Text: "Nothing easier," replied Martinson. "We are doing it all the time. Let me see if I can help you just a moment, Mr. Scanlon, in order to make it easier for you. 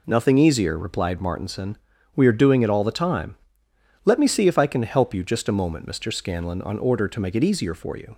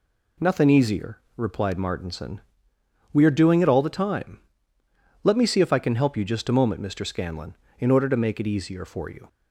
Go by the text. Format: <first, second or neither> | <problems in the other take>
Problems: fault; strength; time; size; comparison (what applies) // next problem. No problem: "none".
second | says "on" for "in"; at 6.6 s